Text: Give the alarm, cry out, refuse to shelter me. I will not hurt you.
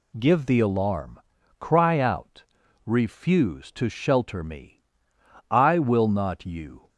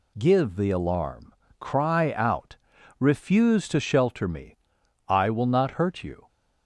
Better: second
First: skips "hurt"; at 6.4 s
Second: none

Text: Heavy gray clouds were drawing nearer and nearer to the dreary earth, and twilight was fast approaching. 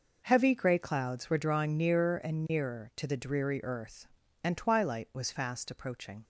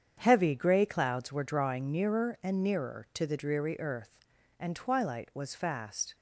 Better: first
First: none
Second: starts louder than the rest; strong; until 1.2 s; 8 dB // stops before "approaching"; at 6.1 s

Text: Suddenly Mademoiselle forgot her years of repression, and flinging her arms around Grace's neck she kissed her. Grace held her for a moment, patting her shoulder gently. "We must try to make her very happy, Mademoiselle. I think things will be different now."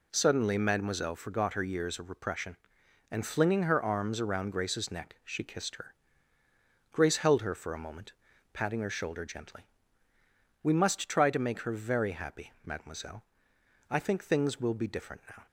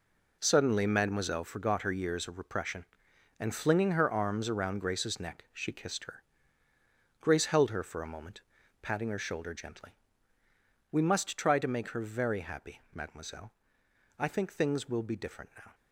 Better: first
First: none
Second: gets quieter; strong; throughout; 10.5 dB

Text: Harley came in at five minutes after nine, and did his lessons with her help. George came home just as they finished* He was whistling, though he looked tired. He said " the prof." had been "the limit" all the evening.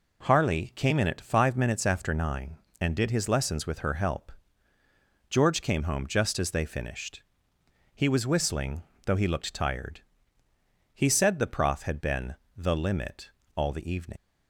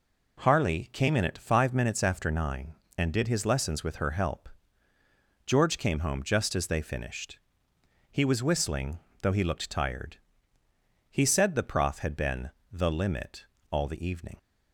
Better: second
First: pauses between "finished" and "He"; noticeable; at 7.2 s; 0.72 s long // pauses between "been" and "the"; slight; at 12.3 s; 0.20 s long // pauses between "limit" and "all"; slight; at 13.3 s; 0.26 s long // leaves "evening" unfinished; at 14.1 s; 60 ms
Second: pauses between "finished" and "He"; noticeable; at 7.3 s; 0.72 s long // pauses between "been" and "the"; slight; at 12.5 s; 0.20 s long // pauses between "limit" and "all"; slight; at 13.4 s; 0.26 s long

